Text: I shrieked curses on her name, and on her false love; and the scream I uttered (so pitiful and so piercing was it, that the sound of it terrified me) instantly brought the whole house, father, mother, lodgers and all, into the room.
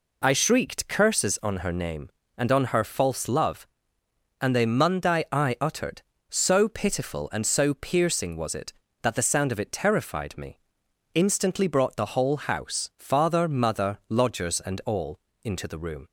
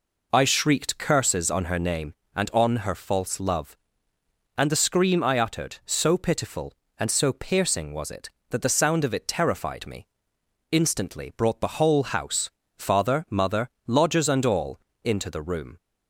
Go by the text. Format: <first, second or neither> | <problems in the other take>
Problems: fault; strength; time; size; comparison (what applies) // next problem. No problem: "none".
second | says "mundi" for "scream"; at 4.6 s